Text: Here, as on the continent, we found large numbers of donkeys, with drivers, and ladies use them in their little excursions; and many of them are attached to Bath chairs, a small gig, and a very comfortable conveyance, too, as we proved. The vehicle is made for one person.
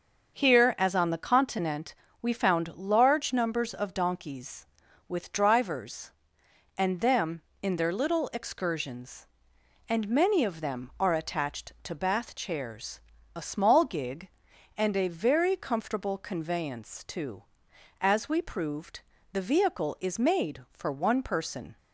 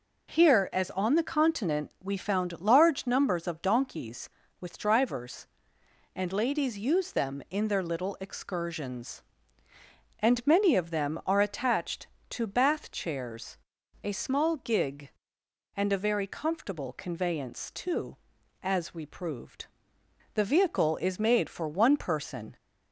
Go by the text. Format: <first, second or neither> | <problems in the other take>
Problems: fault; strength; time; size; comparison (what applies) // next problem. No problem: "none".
second | starts louder than the rest; until 1.3 s; 6.5 dB // skips "ladies use"; at 6.9 s